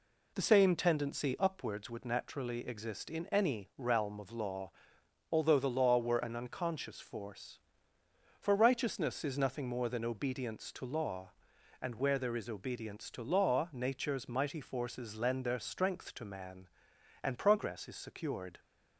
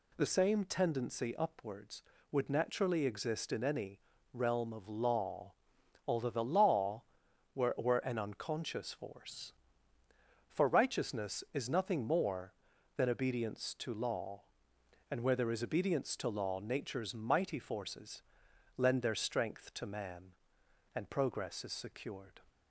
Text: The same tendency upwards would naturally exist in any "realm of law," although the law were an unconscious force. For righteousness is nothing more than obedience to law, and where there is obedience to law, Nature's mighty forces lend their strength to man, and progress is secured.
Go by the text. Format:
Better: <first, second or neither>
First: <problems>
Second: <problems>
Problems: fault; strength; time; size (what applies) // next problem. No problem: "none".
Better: first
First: none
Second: pauses between "any" and "realm"; slight; at 3.9 s; 0.32 s long // says "were" twice; at 7.7 s // pauses between "forces" and "lend"; noticeable; at 18.2 s; 0.56 s long